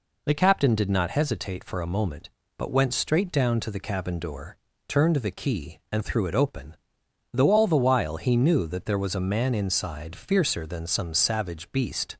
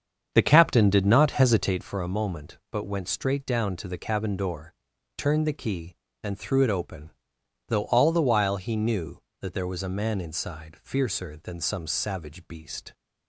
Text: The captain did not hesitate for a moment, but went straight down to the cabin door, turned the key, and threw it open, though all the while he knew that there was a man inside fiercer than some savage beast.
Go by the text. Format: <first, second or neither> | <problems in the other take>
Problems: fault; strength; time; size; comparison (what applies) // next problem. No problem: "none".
first | starts louder than the rest; strong; until 1.9 s; 7.5 dB